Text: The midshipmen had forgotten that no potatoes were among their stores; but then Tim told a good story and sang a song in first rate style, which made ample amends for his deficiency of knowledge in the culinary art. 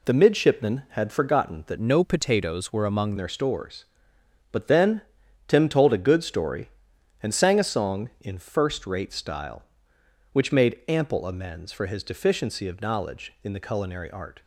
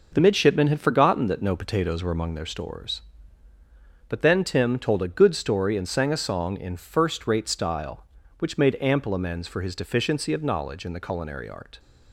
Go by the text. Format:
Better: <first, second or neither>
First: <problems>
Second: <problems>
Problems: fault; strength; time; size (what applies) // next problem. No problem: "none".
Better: second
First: changes voice from "no" to "among"; from 1.7 to 3.1 s; 1.4 s long // pauses between "then" and "Tim"; noticeable; at 4.9 s; 0.48 s long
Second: none